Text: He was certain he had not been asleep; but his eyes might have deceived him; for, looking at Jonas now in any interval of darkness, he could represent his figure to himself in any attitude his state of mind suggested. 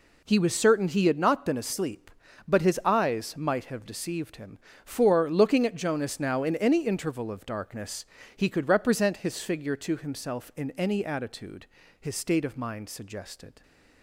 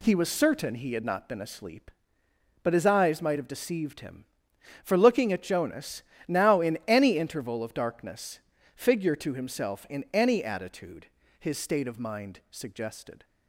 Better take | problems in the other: first | pauses between "Jonas" and "now"; slight; at 6.0 s; 0.26 s long // skips "he could represent his"; at 8.5 s // pauses between "attitude" and "his"; slight; at 11.0 s; 0.34 s long; slight in the first

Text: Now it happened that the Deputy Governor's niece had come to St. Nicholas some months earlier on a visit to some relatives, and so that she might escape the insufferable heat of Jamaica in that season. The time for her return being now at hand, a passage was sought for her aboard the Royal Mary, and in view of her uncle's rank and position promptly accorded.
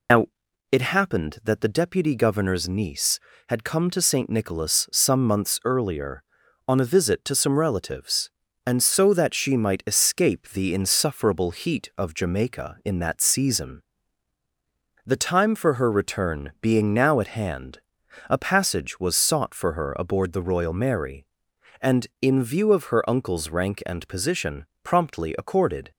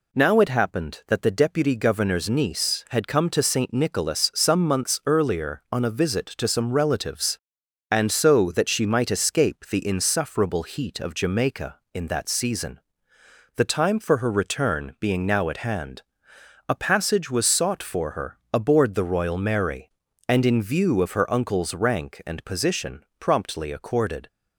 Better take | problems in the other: second | loses the start of "Now"; at 0.0 s; 85 ms // pauses between "Now" and "it"; at 0.2 s; 0.44 s long // pauses between "position" and "promptly"; slight; at 24.6 s; 0.18 s long

